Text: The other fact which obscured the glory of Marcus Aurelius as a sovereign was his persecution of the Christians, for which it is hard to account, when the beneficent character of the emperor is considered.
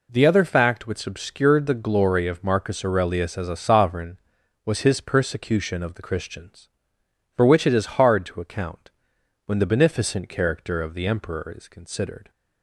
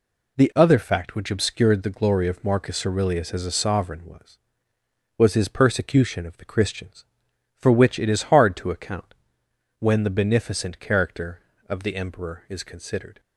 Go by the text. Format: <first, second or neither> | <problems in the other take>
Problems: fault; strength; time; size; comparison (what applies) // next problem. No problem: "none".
first | says "was" twice; at 5.1 s